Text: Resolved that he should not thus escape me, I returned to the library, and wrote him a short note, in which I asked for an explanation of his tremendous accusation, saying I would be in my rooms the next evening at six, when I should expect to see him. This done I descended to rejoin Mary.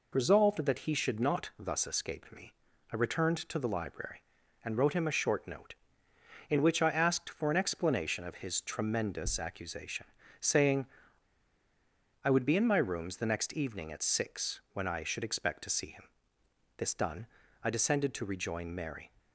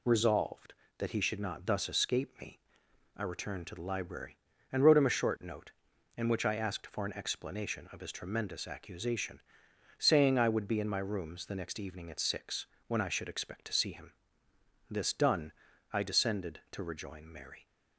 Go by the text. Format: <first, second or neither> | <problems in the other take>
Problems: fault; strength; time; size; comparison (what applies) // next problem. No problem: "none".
second | pauses between "saying" and "I"; strong; at 10.8 s; 1.3 s long // pauses between "done" and "I"; slight; at 17.2 s; 0.36 s long; also in the second